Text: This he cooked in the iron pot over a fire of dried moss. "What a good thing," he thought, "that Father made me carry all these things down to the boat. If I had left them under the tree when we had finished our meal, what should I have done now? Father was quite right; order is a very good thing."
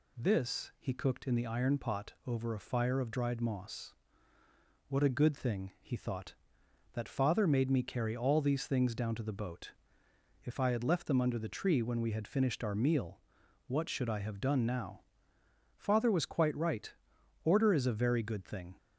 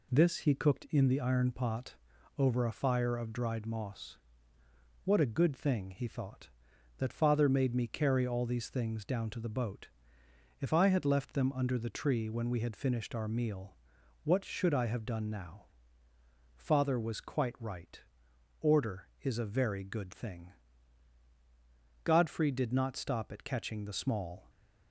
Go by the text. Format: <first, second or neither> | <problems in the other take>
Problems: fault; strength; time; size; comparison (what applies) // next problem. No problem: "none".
first | pauses between "pot" and "over"; at 1.9 s; 0.44 s long // goes on to say "Godfrey did not stop at catching the small"; strong; from 22.0 s on; 2.4 s long // stays silent after the last word; slight; from 24.4 s on; 0.5 s long